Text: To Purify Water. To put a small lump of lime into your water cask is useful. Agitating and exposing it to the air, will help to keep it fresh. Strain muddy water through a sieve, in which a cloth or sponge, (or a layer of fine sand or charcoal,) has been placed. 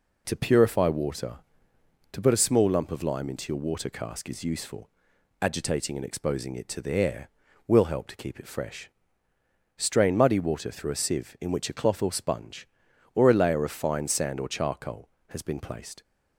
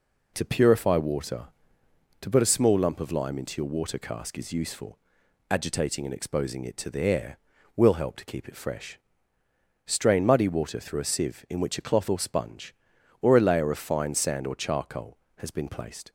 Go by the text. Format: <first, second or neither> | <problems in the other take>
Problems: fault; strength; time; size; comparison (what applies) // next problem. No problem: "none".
neither | none